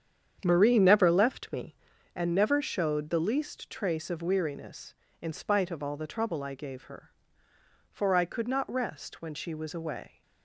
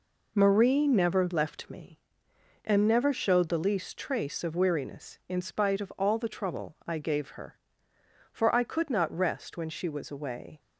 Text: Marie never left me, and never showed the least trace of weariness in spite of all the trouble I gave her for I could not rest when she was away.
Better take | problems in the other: second | starts louder than the rest; strong; until 2.1 s; 8.5 dB

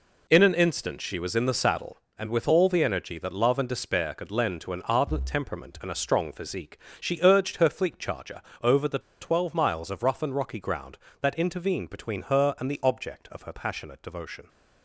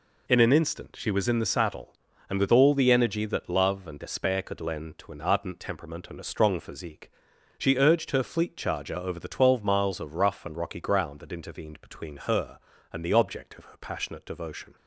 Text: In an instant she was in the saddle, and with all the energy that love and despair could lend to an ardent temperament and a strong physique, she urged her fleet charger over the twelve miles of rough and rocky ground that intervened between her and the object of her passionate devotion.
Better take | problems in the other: second | pauses between "charger" and "over"; slight; at 8.4 s; 0.20 s long // pauses between "the" and "twelve"; slight; at 8.9 s; 0.21 s long

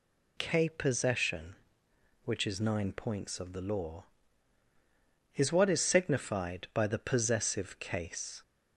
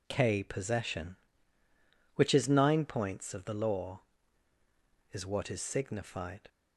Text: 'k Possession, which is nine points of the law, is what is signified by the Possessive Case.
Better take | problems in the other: first | stops before "by the Possessive Case"; at 6.4 s

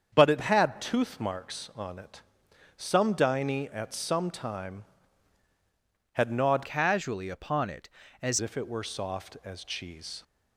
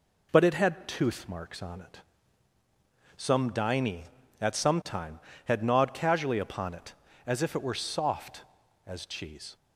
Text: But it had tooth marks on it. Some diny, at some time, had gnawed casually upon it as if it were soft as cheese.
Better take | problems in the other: second | starts louder than the rest; strong; until 1.1 s; 7.5 dB // changes voice from "casually" to "as"; from 6.6 to 8.3 s; 1.7 s long

